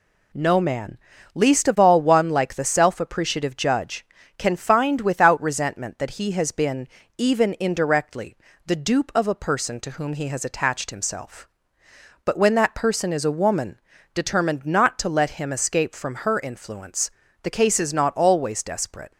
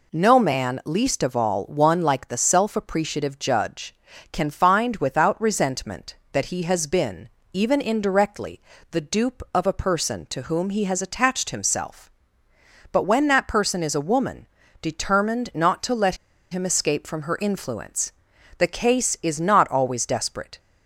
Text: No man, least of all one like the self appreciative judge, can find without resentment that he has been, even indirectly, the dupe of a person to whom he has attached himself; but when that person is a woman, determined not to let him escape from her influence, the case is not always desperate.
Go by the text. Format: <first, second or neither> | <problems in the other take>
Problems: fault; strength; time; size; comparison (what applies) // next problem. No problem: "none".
first | pauses between "let" and "him"; slight; at 16.1 s; 0.36 s long